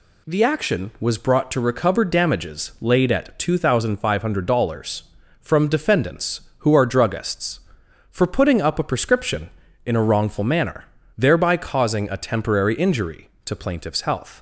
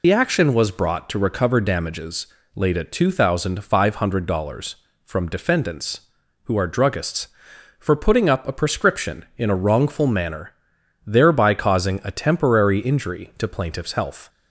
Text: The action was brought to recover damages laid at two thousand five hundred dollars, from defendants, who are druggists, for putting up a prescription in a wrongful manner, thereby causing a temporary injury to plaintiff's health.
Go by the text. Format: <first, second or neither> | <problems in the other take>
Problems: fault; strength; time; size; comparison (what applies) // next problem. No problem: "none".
first | loses the start of "The"; at 0.0 s; 80 ms // pauses between "damages" and "laid"; slight; at 2.2 s; 0.28 s long